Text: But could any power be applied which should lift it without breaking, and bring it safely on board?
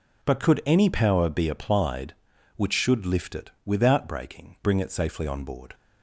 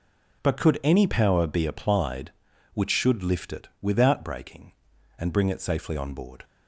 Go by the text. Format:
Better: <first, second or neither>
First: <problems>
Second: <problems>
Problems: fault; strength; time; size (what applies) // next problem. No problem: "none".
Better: second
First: pauses between "it" and "without"; slight; at 3.4 s; 0.16 s long // skips "and"; at 4.5 s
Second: none